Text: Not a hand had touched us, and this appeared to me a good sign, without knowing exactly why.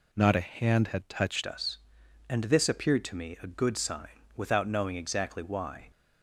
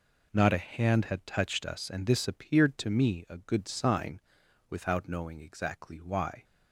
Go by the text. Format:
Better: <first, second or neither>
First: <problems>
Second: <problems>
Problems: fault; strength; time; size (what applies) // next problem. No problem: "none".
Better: second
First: changes voice at "us"; from 1.4 s on; 4.5 s long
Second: none